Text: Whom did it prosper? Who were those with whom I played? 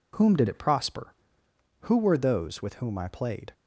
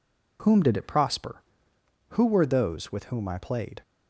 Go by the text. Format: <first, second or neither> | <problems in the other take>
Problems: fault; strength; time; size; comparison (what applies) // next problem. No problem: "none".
neither | none